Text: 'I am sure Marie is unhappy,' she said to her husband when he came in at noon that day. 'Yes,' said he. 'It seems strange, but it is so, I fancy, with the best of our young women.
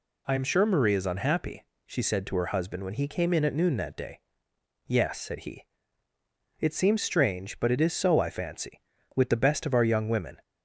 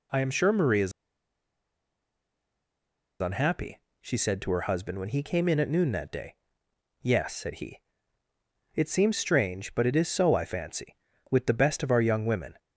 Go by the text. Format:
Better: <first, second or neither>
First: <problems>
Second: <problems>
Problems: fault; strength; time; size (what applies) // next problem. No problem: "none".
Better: first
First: none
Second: pauses between "is" and "unhappy"; strong; at 0.9 s; 2.3 s long